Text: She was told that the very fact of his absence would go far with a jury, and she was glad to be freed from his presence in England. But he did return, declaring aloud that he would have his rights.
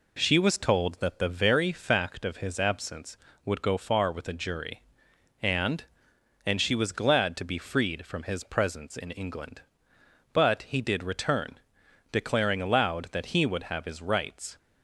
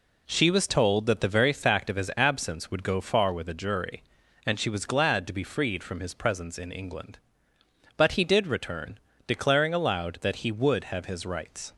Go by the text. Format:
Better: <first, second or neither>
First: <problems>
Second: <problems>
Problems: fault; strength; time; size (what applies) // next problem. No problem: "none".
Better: second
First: says "and" twice; at 6.4 s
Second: none